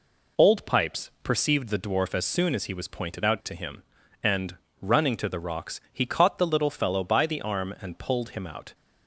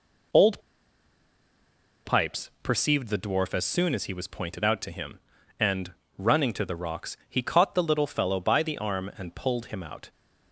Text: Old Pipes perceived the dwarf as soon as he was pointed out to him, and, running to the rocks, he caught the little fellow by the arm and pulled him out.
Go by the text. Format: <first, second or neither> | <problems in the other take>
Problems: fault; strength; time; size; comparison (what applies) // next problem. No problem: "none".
first | pauses between "Old" and "Pipes"; strong; at 0.6 s; 1.4 s long